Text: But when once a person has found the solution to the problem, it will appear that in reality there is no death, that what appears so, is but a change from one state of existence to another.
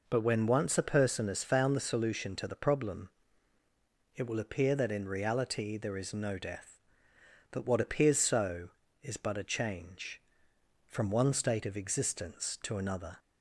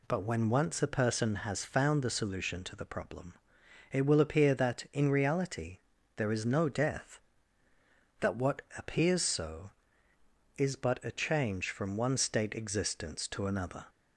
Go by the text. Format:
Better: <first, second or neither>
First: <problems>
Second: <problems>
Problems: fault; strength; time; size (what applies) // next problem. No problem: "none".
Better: first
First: none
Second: pauses between "reality" and "there"; at 5.7 s; 0.38 s long // skips "of"; at 12.5 s